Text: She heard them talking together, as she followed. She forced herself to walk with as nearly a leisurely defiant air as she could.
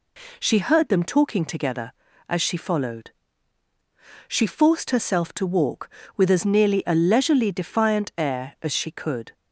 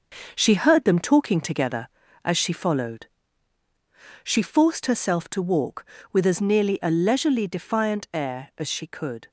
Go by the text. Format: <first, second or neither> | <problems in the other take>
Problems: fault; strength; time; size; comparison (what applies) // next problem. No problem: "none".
first | gets quieter; throughout; 6 dB